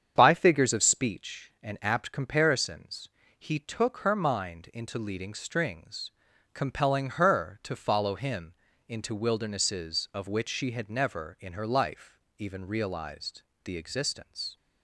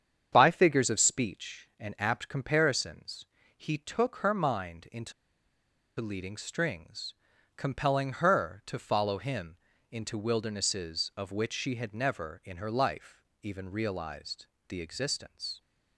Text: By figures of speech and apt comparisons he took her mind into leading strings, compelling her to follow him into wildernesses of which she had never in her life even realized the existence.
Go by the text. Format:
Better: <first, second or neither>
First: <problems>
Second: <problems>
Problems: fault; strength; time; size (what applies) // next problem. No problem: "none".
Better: first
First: starts louder than the rest; strong; until 1.1 s; 8 dB // pauses between "comparisons" and "he"; slight; at 3.0 s; 0.28 s long // pauses between "him" and "into"; slight; at 8.5 s; 0.34 s long // pauses between "life" and "even"; slight; at 12.1 s; 0.18 s long // pauses between "realized" and "the"; slight; at 13.4 s; 0.22 s long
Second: starts louder than the rest; strong; until 1.3 s; 8 dB // pauses between "comparisons" and "he"; slight; at 3.2 s; 0.30 s long // pauses between "into" and "leading"; noticeable; at 5.1 s; 0.87 s long // pauses between "him" and "into"; slight; at 9.5 s; 0.34 s long // pauses between "life" and "even"; slight; at 13.2 s; 0.18 s long // pauses between "realized" and "the"; slight; at 14.4 s; 0.22 s long